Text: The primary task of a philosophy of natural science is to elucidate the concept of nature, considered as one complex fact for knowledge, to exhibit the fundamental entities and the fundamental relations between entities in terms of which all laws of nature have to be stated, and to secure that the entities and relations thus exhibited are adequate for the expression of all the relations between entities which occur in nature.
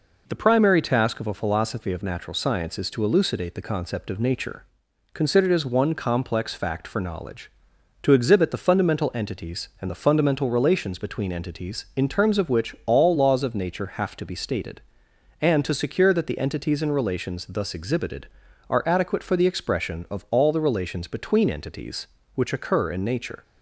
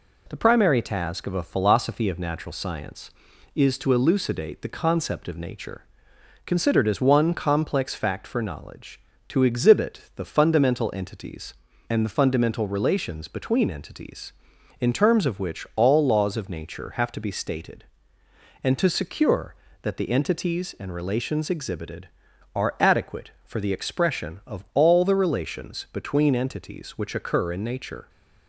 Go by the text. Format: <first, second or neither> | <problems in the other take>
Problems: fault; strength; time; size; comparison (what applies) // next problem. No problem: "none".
first | skips "thus"; at 21.4 s